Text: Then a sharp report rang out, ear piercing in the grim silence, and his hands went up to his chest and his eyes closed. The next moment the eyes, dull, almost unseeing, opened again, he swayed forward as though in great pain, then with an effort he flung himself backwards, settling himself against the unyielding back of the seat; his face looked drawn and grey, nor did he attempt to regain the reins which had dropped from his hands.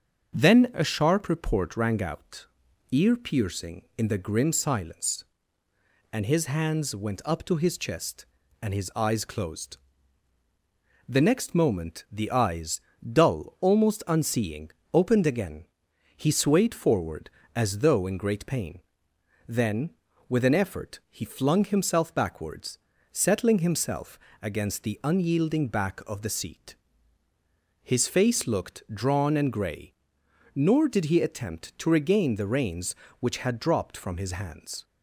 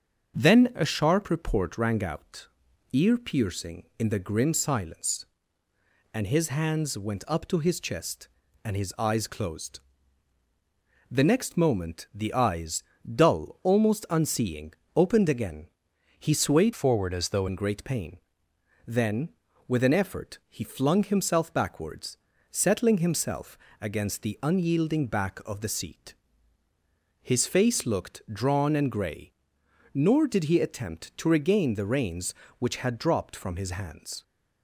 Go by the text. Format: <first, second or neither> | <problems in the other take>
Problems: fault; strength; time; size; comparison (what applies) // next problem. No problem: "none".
first | starts louder than the rest; strong; until 1.4 s; 7 dB; also in the first // changes voice from "forward" to "though"; from 16.7 to 17.4 s; 0.7 s long // pauses between "himself" and "against"; slight; at 23.5 s; 0.24 s long; slight in the first